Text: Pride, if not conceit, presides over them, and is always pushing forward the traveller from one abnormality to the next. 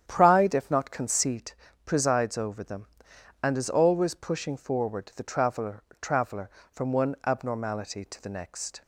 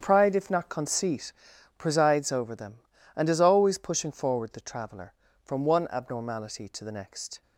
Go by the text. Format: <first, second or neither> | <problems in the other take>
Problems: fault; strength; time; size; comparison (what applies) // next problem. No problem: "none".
second | starts louder than the rest; strong; until 1.0 s; 9 dB; strong in the second // says "traveller" twice; at 5.9 s